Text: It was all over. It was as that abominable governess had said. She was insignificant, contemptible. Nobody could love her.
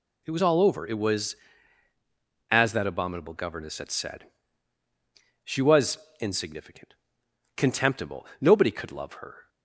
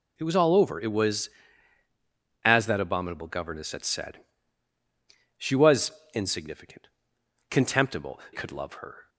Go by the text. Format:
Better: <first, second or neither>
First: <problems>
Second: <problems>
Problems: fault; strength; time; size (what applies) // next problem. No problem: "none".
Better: first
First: pauses between "was" and "insignificant"; slight; at 5.9 s; 0.22 s long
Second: pauses between "was" and "insignificant"; slight; at 5.9 s; 0.22 s long // skips "Nobody"; at 8.2 s